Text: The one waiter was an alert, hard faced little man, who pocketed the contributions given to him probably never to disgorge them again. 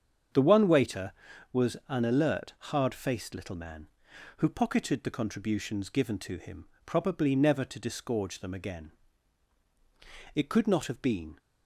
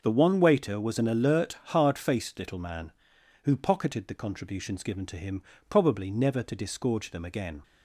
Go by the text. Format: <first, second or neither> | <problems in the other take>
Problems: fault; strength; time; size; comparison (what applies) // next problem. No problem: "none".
second | starts louder than the rest; strong; until 1.7 s; 7.5 dB // pauses between "him" and "probably"; slight; at 6.6 s; 0.20 s long; slight in the second // goes on to say "It could not have been"; noticeable; from 10.3 s on; 1.0 s long